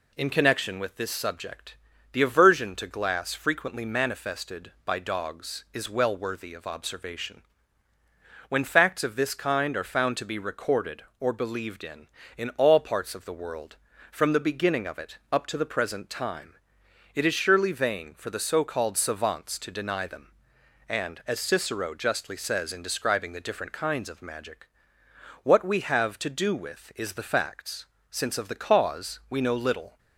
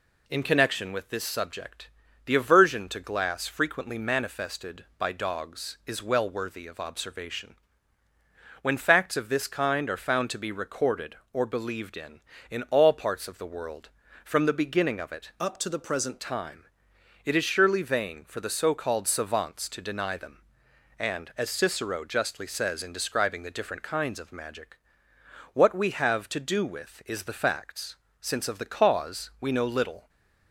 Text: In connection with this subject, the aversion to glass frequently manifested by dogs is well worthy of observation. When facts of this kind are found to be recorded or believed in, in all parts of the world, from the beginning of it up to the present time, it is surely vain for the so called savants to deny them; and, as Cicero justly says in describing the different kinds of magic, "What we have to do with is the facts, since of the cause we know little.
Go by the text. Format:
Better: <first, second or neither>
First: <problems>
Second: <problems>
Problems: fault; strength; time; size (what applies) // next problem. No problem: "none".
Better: first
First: none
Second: changes voice from "up" to "present"; from 15.4 to 16.1 s; 0.7 s long // stays silent after the last word; slight; from 30.0 s on; 0.5 s long